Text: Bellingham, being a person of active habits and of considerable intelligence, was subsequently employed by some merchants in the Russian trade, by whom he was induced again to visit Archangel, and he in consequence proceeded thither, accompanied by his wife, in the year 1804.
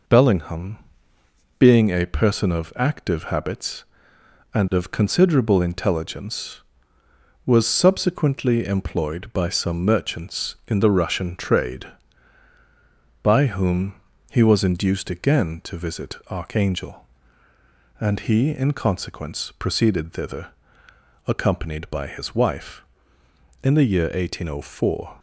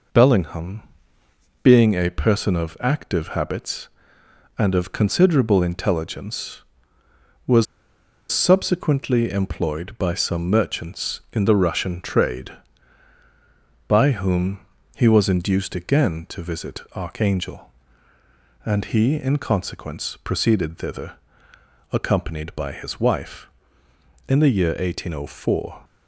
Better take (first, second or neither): first